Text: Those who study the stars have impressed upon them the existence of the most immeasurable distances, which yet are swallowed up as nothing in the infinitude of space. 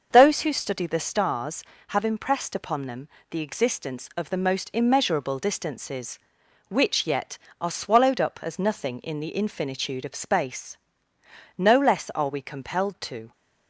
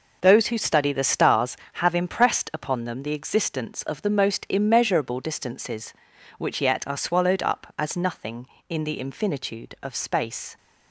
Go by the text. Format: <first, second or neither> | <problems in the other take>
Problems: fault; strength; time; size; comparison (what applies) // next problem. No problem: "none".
second | starts louder than the rest; noticeable; until 1.1 s; 6 dB // pauses between "them" and "the"; slight; at 3.0 s; 0.22 s long // goes on to say "No less are we compelled to"; strong; from 11.5 s on; 1.7 s long